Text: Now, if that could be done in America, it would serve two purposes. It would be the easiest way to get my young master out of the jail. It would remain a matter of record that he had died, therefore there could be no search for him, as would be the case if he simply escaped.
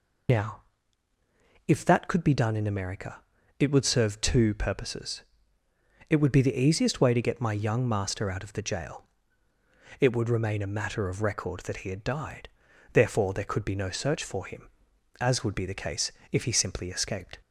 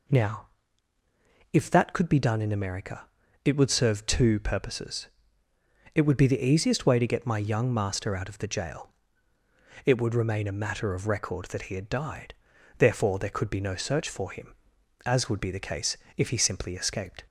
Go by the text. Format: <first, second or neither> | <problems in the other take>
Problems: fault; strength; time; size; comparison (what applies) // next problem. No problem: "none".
second | loses the start of "Now"; at 0.2 s; 55 ms // pauses between "case" and "if"; slight; at 16.1 s; 0.20 s long; slight in the second